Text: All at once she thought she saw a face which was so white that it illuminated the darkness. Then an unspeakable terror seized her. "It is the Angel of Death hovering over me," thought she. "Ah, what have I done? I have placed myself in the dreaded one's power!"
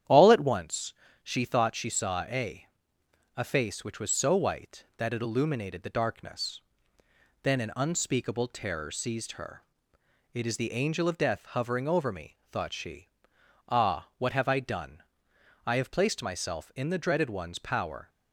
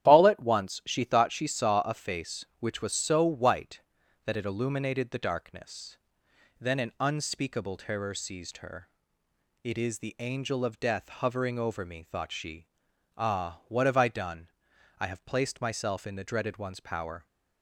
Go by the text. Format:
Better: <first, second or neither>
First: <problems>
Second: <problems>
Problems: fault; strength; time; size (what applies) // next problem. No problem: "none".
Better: second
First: starts louder than the rest; strong; until 1.3 s; 10 dB // pauses between "once" and "she"; slight; at 0.9 s; 0.30 s long // says "a" twice; at 3.3 s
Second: starts louder than the rest; strong; until 1.1 s; 11 dB